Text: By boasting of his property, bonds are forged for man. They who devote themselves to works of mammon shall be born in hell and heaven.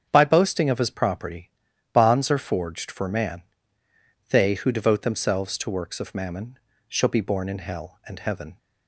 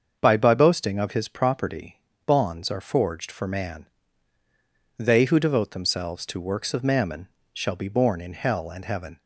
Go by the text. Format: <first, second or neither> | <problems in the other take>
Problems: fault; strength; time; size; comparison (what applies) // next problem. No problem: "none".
first | starts louder than the rest; until 1.2 s; 6.5 dB; strong in the first // says "By" twice; at 0.3 s // pauses between "mammon" and "shall"; slight; at 7.2 s; 0.26 s long; slight in the first